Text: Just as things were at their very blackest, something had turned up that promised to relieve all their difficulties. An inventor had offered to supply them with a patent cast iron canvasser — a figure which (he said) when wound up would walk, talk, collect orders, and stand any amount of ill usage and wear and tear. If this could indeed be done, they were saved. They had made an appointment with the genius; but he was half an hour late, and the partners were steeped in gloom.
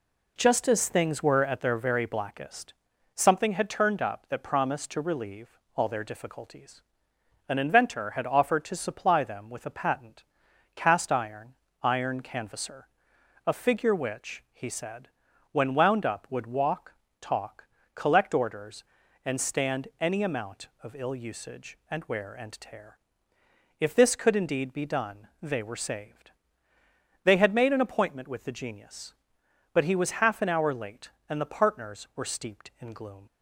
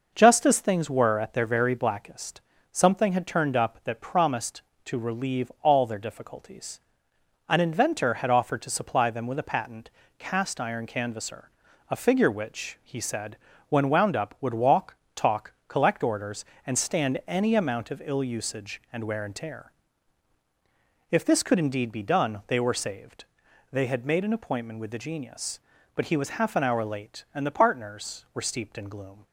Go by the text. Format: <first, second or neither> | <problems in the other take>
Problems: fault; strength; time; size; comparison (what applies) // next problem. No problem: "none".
second | pauses between "relieve" and "all"; slight; at 5.5 s; 0.18 s long // pauses between "patent" and "cast"; noticeable; at 10.2 s; 0.52 s long; slight in the second // says "iron" twice; at 11.8 s